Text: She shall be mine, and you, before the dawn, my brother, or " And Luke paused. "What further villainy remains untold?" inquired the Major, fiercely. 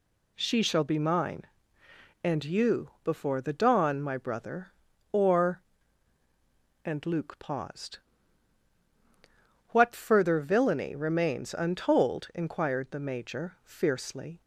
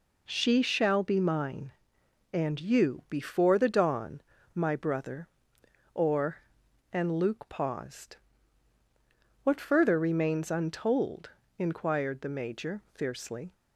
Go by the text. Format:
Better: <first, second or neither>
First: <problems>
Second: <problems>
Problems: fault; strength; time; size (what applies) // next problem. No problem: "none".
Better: first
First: none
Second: skips "villainy"; at 9.9 s